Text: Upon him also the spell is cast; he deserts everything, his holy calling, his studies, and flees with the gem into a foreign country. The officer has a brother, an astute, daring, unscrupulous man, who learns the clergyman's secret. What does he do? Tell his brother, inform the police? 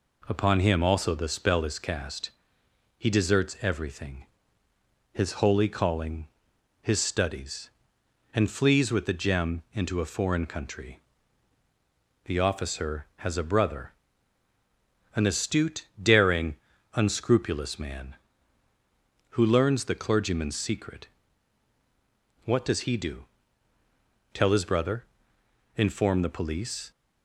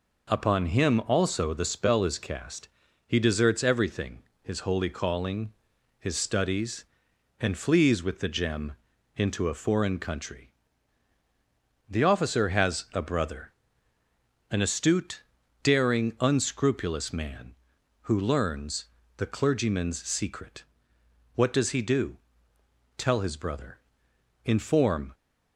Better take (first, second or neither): first